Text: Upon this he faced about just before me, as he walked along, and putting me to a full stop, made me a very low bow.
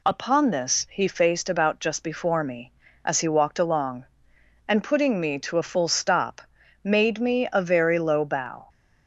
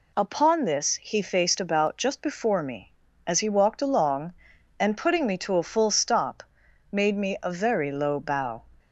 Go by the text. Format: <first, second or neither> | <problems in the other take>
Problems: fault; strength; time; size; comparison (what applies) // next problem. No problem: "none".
neither | none